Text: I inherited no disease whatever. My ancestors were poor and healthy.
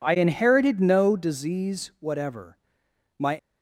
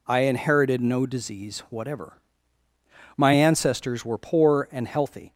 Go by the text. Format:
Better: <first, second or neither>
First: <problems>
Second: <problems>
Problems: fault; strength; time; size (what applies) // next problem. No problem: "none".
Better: second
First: stops before "ancestors were poor and healthy"; at 3.3 s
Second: none